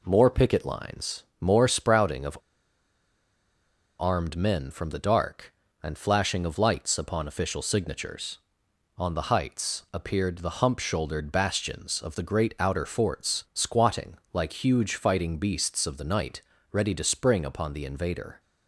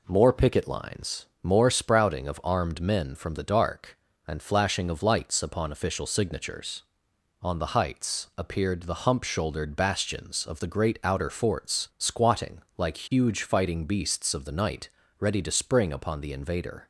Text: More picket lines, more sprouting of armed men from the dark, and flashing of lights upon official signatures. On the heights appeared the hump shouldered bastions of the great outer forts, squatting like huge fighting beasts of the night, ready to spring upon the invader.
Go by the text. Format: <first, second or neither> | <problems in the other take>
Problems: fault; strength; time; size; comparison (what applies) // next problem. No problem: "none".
second | pauses between "of" and "armed"; strong; at 2.3 s; 1.6 s long // pauses between "squatting" and "like"; slight; at 14.1 s; 0.16 s long; slight in the second